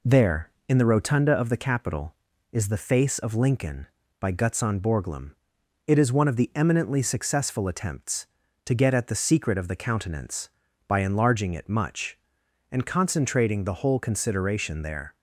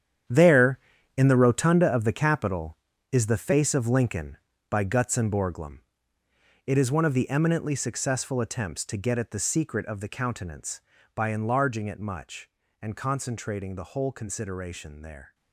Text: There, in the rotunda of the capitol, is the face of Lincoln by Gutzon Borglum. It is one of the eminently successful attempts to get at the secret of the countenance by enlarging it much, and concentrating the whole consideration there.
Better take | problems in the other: first | gets quieter; strong; throughout; 12 dB

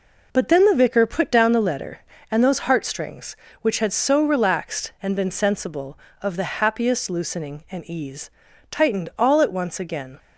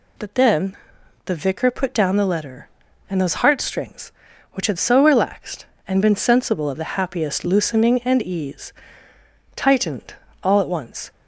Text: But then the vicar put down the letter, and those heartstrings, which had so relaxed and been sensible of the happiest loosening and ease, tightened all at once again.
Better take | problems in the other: first | pauses between "then" and "the"; noticeable; at 0.7 s; 0.50 s long // pauses between "tightened" and "all"; slight; at 10.1 s; 0.28 s long // stops before "again"; at 11.1 s

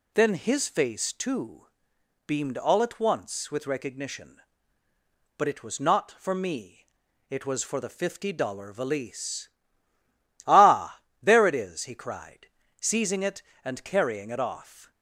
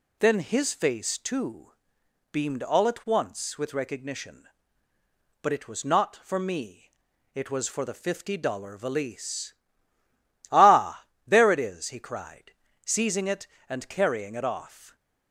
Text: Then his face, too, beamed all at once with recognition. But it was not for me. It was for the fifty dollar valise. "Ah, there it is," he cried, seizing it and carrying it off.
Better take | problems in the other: neither | none

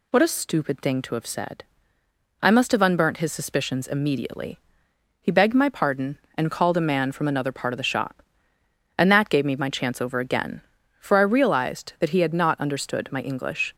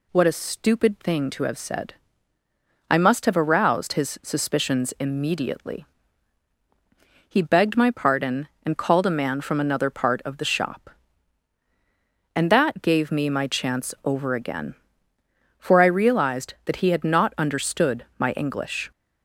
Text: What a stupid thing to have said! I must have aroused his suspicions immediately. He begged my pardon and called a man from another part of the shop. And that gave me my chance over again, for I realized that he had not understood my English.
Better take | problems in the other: second | says "unburnt" for "aroused"; at 2.8 s

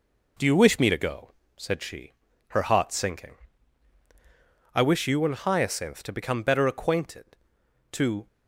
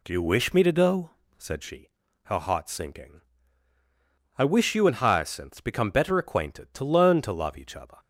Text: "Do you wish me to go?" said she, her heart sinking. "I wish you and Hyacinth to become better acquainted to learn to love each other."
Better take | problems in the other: second | stops before "learn to love each other"; at 8.2 s

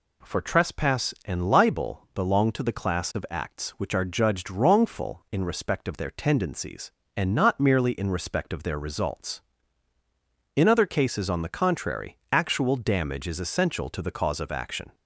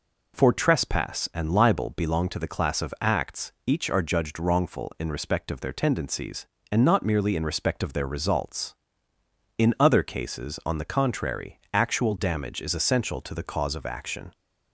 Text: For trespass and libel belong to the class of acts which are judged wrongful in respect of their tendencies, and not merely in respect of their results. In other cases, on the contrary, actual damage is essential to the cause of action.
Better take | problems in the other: first | says "each" for "which"; at 3.6 s

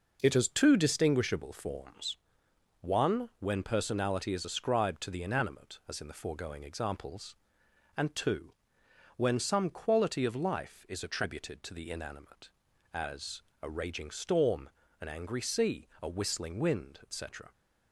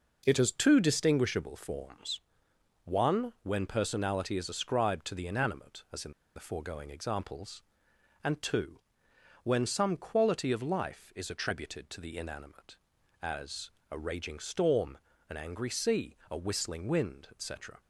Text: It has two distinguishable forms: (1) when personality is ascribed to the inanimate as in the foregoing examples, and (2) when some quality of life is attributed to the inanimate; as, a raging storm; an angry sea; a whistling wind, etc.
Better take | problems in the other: first | pauses between "in" and "the"; slight; at 6.1 s; 0.23 s long

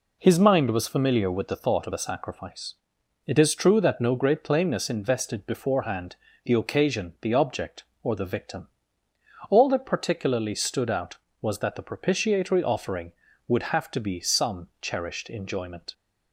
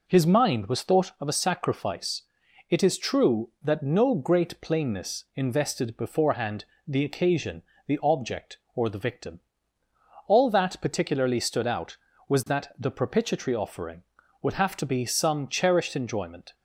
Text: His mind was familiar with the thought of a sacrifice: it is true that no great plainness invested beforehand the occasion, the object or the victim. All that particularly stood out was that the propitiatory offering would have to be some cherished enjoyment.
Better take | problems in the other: first | skips "familiar with the"; at 0.8 s // pauses between "beforehand" and "the"; slight; at 6.6 s; 0.22 s long; slight in the first

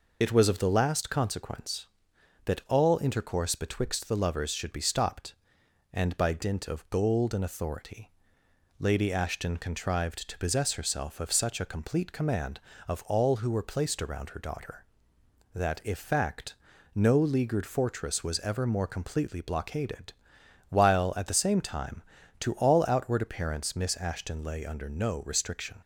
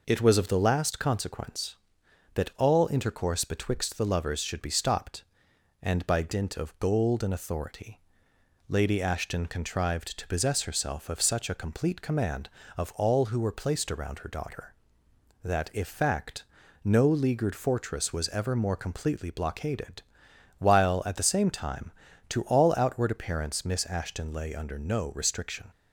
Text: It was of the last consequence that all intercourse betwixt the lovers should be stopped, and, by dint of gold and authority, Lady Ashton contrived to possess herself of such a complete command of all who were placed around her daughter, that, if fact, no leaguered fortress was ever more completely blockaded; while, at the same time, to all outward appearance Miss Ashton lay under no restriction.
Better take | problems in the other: second | loses the start of "It"; at 0.2 s; 35 ms

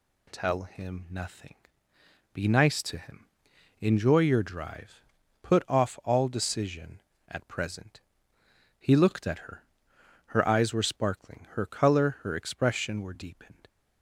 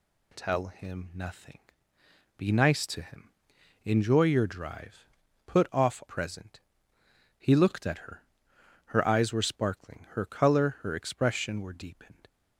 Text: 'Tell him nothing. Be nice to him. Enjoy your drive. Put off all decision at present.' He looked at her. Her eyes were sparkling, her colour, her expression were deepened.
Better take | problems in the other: first | skips "all decision at"; at 6.0 s

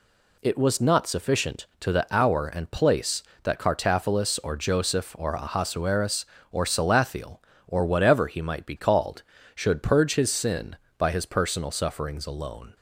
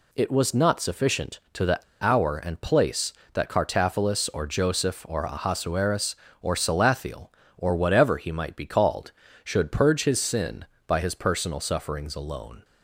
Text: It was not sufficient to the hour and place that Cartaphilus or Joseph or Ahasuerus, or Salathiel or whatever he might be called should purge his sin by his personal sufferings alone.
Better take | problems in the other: first | pauses between "the" and "hour"; slight; at 1.7 s; 0.22 s long

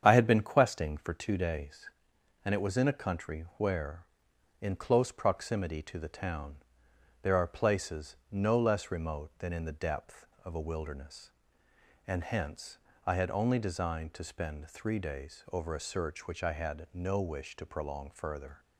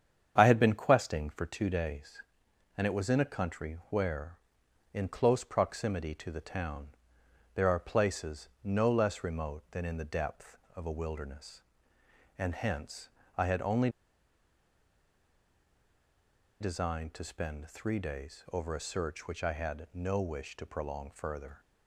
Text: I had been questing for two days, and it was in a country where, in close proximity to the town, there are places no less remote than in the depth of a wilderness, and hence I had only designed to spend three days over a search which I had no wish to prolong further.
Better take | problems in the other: first | starts louder than the rest; strong; until 1.3 s; 8 dB; strong in the first // pauses between "hence" and "I"; slight; at 13.0 s; 0.30 s long; slight in the first // pauses between "only" and "designed"; strong; at 13.8 s; 2.7 s long

